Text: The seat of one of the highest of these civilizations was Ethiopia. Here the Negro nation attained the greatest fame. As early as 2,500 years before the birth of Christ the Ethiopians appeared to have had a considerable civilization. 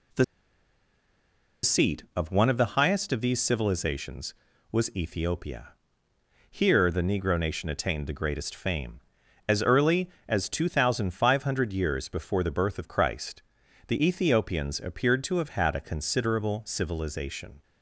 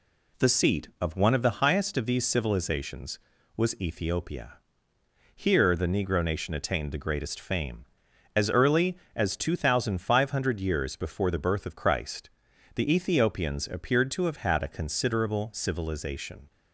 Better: second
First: pauses between "The" and "seat"; strong; at 0.2 s; 1.3 s long // pauses between "Christ" and "the"; noticeable; at 13.4 s; 0.46 s long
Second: pauses between "Christ" and "the"; noticeable; at 12.2 s; 0.46 s long

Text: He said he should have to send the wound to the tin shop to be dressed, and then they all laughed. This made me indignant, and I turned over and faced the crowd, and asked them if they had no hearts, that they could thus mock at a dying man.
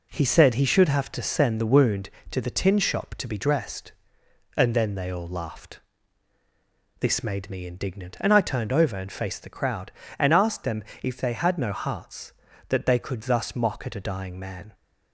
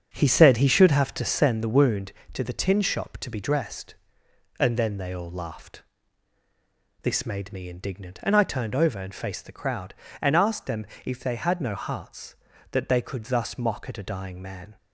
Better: first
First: pauses between "them" and "if"; slight; at 10.8 s; 0.18 s long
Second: starts louder than the rest; until 1.6 s; 7 dB // pauses between "them" and "if"; slight; at 10.8 s; 0.18 s long

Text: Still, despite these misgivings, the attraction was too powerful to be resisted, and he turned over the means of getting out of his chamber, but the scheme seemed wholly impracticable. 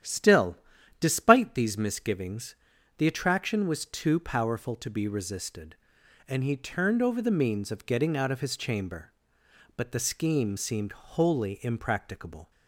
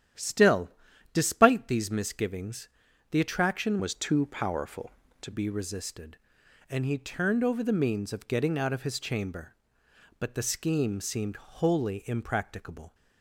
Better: first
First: starts louder than the rest; strong; until 1.4 s; 10.5 dB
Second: starts louder than the rest; strong; until 1.5 s; 10.5 dB // changes voice from "was" to "to"; from 3.7 to 5.3 s; 1.6 s long

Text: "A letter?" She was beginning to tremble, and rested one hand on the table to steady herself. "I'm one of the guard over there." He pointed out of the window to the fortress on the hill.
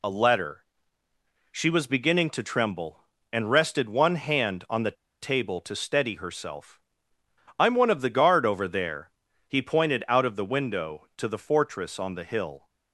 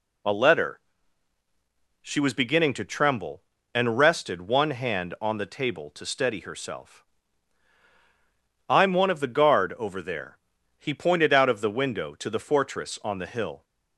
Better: second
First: pauses between "the" and "table"; slight; at 4.9 s; 0.28 s long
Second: none

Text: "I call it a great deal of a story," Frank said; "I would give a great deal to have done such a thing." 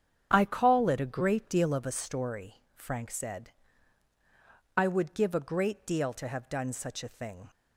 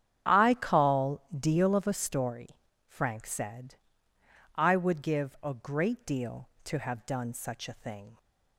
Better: first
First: starts louder than the rest; strong; until 1.3 s; 7.5 dB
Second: starts louder than the rest; strong; until 1.4 s; 9.5 dB // skips "it a great"; at 1.2 s

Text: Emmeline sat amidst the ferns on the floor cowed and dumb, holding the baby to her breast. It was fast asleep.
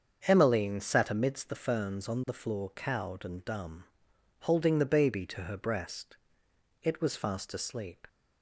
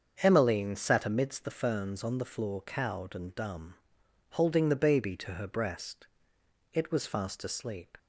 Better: neither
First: starts louder than the rest; until 1.2 s; 7 dB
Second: starts louder than the rest; until 1.2 s; 7 dB

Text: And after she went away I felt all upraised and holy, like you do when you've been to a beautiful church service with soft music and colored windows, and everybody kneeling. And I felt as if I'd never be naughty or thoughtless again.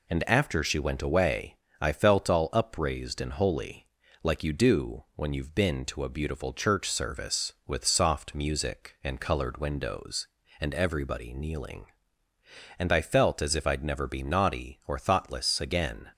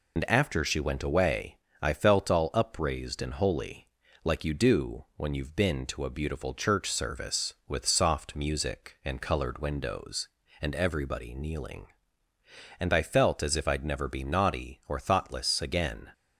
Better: first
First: pauses between "away" and "I"; slight; at 1.5 s; 0.26 s long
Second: loses the start of "And"; at 0.1 s; 55 ms // pauses between "away" and "I"; slight; at 1.5 s; 0.26 s long

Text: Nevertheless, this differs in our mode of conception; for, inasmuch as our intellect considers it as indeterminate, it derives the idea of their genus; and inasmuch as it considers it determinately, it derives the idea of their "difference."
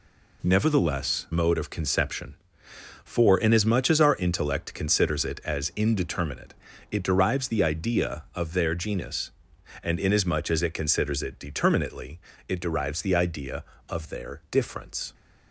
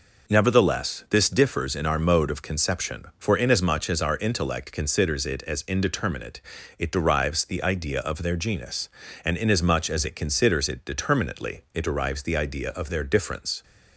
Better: second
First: skips "this differs in our"; at 1.2 s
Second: none

